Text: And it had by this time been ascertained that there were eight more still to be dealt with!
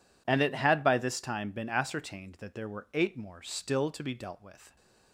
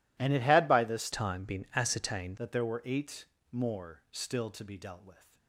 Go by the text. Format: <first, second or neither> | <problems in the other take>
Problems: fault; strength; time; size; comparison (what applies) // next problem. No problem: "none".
first | changes voice from "time" to "ascertained"; from 1.1 to 2.3 s; 1.2 s long // pauses between "eight" and "more"; slight; at 3.2 s; 0.26 s long